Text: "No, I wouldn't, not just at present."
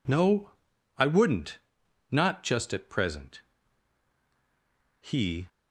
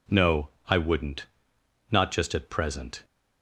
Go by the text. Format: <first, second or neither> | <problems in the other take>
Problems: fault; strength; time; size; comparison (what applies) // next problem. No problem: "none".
second | goes on to say "He"; slight; from 5.0 s on; 0.48 s long